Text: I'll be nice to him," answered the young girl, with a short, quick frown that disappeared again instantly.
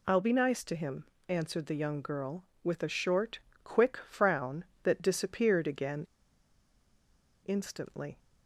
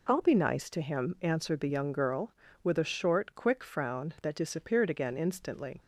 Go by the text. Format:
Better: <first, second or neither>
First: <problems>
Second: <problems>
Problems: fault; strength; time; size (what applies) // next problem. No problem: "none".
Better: second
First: pauses between "again" and "instantly"; strong; at 6.0 s; 1.3 s long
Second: none